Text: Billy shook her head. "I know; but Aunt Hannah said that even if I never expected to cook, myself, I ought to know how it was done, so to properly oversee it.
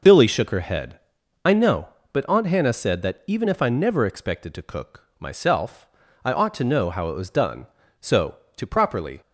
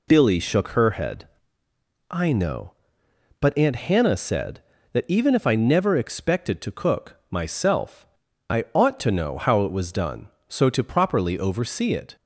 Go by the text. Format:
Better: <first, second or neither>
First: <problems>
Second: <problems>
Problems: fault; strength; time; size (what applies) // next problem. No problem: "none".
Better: second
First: stops before "oversee it"; at 9.2 s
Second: none